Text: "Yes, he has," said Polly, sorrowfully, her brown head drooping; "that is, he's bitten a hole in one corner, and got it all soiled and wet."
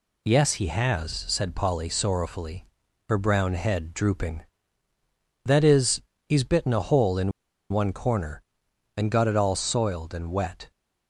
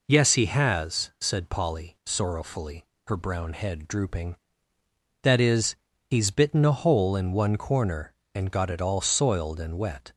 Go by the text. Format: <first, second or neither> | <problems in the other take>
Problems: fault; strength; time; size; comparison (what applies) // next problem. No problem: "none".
second | pauses between "in" and "one"; at 7.3 s; 0.41 s long